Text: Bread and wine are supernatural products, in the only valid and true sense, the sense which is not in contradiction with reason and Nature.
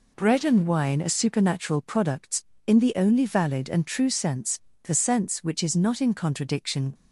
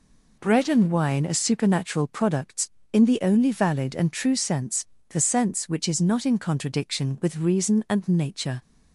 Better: second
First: stops before "with reason and Nature"; at 6.9 s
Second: none

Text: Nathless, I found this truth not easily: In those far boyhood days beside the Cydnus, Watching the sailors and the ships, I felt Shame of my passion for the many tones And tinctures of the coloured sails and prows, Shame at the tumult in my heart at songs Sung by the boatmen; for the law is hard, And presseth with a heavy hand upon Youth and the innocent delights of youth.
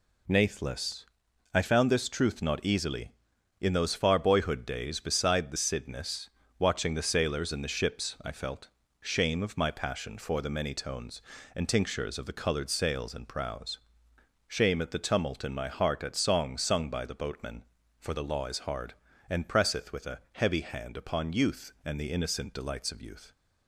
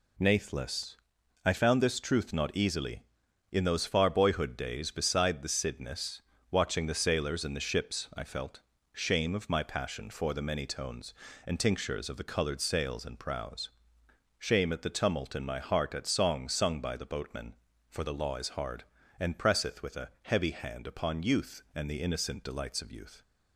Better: neither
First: pauses between "felt" and "Shame"; slight; at 8.6 s; 0.32 s long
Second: pauses between "felt" and "Shame"; slight; at 8.6 s; 0.32 s long

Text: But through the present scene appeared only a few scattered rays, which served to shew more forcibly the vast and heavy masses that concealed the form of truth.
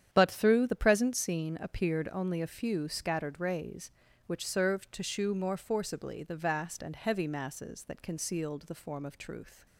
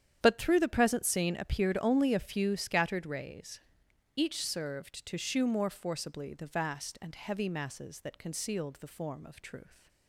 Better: first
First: starts louder than the rest; strong; until 1.1 s; 9.5 dB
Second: starts louder than the rest; strong; until 1.2 s; 9.5 dB // says "each" for "which"; at 4.1 s

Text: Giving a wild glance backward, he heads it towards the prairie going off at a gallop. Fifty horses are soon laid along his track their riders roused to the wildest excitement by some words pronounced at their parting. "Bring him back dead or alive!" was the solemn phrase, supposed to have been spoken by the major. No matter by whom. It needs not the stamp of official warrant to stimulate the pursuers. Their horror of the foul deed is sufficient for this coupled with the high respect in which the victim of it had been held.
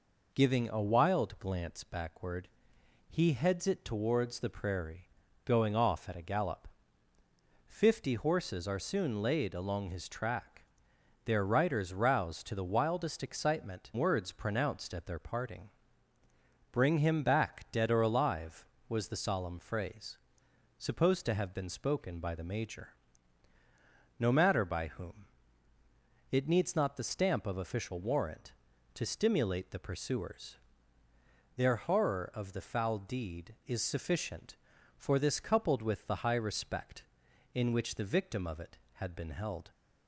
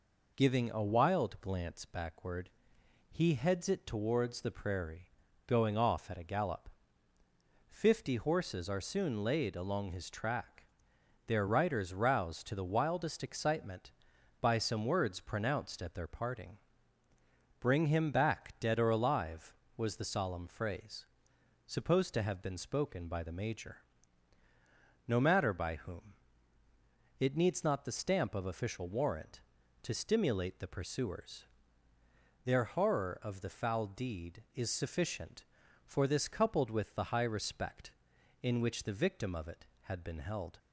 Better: second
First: pauses between "prairie" and "going"; slight; at 5.0 s; 0.36 s long // pauses between "track" and "their"; noticeable; at 10.6 s; 0.60 s long // skips "by some"; at 13.9 s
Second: pauses between "prairie" and "going"; slight; at 5.0 s; 0.36 s long // pauses between "track" and "their"; noticeable; at 10.6 s; 0.60 s long

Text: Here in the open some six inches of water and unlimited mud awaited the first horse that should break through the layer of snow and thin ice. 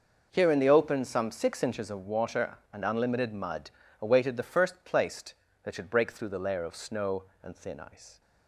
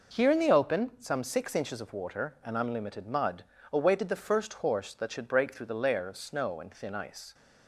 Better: second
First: pauses between "mud" and "awaited"; slight; at 3.7 s; 0.28 s long // says "placed" for "horse"; at 4.8 s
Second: pauses between "mud" and "awaited"; slight; at 3.4 s; 0.28 s long

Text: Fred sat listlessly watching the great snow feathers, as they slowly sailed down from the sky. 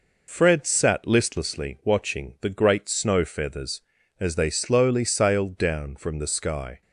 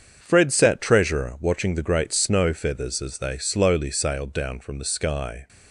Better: first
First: none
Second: starts louder than the rest; strong; until 1.2 s; 7 dB // says "treasurer" for "listlessly"; at 0.7 s

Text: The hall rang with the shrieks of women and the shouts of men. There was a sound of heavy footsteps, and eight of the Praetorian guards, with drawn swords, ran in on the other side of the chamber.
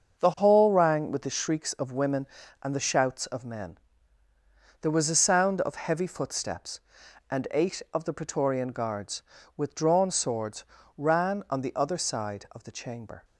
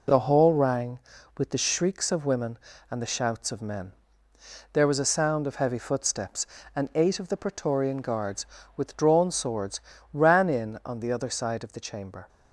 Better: second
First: starts louder than the rest; until 1.2 s; 7 dB // skips "in"; at 11.4 s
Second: none

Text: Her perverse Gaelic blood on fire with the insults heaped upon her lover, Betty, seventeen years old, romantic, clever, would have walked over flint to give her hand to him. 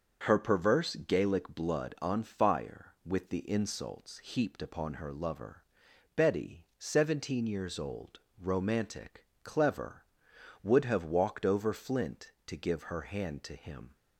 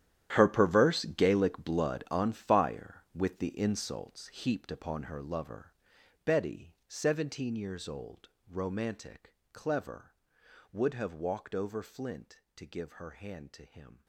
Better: first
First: starts louder than the rest; until 1.2 s; 6.5 dB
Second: gets quieter; strong; throughout; 16 dB // starts louder than the rest; strong; until 1.3 s; 11 dB

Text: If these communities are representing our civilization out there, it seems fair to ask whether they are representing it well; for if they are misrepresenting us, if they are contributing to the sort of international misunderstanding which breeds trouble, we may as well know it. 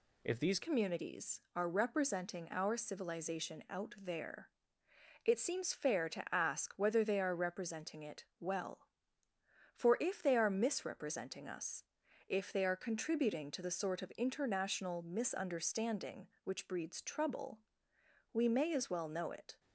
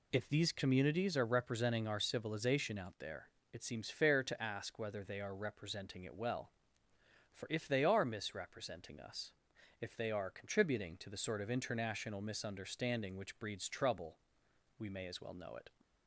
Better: second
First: changes voice at "communities"; from 0.6 s on; 18.9 s long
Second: none

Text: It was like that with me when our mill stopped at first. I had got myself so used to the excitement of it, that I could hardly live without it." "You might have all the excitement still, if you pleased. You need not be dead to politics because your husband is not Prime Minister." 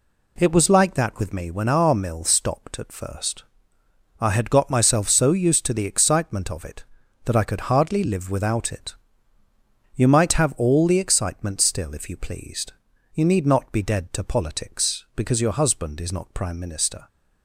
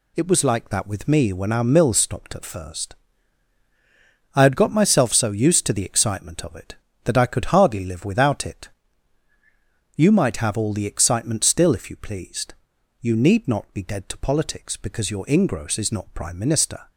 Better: first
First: none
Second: says "ingross" for "husband"; at 15.2 s

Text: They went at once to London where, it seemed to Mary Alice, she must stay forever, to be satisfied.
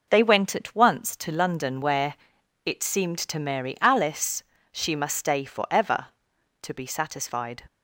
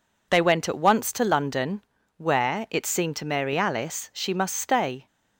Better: first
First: none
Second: pauses between "London" and "where"; at 1.8 s; 0.36 s long // stops before "forever to be satisfied"; at 5.0 s

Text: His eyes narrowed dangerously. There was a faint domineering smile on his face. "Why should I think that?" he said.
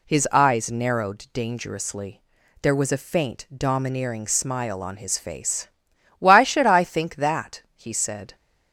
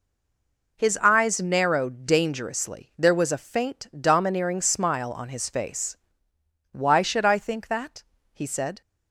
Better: first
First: none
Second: stays silent before the first word; slight; until 0.7 s; 0.7 s long

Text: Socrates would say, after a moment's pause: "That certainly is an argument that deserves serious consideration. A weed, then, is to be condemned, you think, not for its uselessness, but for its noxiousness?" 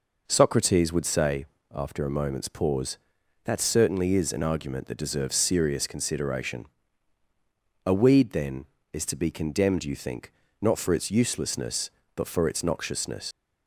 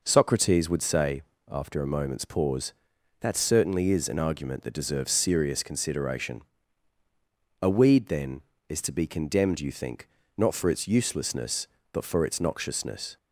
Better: second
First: leaves "noxiousness" unfinished; at 13.3 s; 85 ms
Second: none

